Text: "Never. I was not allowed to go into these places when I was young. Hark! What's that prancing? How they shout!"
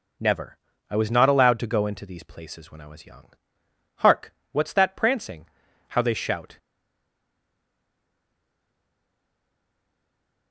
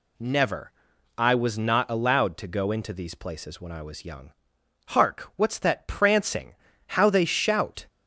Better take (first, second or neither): second